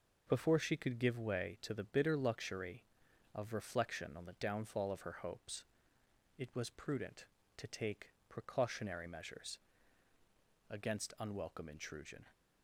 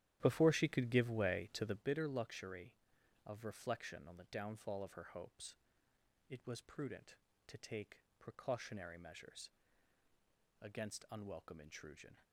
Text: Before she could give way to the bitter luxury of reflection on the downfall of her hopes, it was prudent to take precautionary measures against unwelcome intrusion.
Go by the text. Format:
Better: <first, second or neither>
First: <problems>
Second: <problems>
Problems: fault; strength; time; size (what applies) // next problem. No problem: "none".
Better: first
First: pauses between "take" and "precautionary"; slight; at 8.0 s; 0.18 s long // pauses between "measures" and "against"; at 9.5 s; 1.1 s long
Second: starts louder than the rest; strong; until 1.9 s; 12 dB // pauses between "take" and "precautionary"; slight; at 8.0 s; 0.18 s long // pauses between "measures" and "against"; at 9.4 s; 1.1 s long